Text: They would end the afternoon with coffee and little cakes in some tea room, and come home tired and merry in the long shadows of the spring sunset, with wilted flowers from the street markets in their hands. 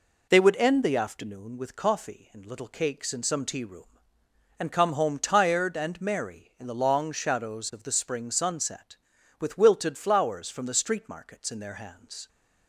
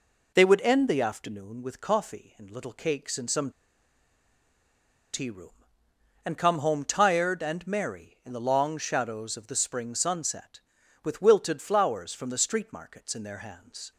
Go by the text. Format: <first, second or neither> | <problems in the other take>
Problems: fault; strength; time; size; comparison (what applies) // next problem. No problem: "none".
first | pauses between "some" and "tea"; strong; at 3.5 s; 1.6 s long